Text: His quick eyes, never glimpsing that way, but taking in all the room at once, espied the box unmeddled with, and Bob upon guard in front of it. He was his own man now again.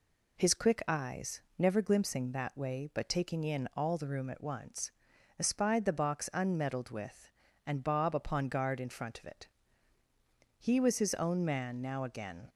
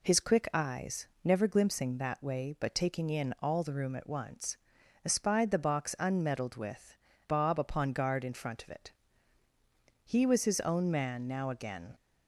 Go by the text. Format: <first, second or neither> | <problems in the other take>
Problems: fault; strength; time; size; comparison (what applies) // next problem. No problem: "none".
first | skips "and"; at 7.1 s